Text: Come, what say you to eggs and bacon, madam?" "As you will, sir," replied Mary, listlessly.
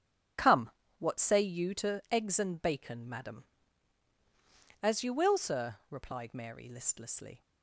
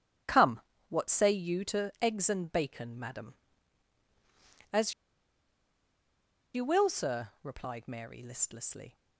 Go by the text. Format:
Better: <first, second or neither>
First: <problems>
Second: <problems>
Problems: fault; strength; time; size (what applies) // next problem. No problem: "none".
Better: first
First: starts louder than the rest; strong; until 1.6 s; 8.5 dB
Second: starts louder than the rest; strong; until 1.5 s; 8.5 dB // pauses between "As" and "you"; strong; at 4.9 s; 1.6 s long